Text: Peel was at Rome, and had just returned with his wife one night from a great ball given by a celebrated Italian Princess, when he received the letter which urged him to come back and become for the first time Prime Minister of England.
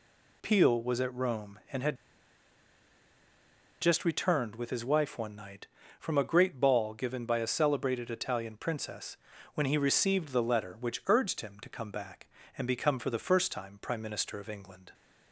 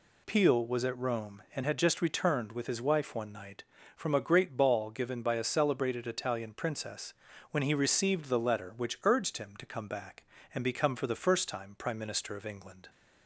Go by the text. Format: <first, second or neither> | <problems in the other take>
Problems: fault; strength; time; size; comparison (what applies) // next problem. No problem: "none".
second | pauses between "had" and "just"; strong; at 1.9 s; 1.8 s long